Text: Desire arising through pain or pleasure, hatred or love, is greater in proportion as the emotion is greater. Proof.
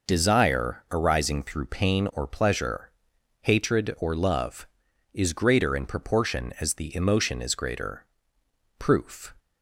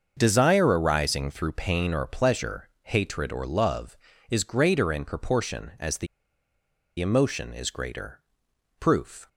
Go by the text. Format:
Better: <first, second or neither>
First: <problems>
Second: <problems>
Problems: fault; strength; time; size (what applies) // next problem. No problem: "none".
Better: first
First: none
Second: starts louder than the rest; until 1.1 s; 6.5 dB // pauses between "the" and "emotion"; noticeable; at 6.0 s; 0.93 s long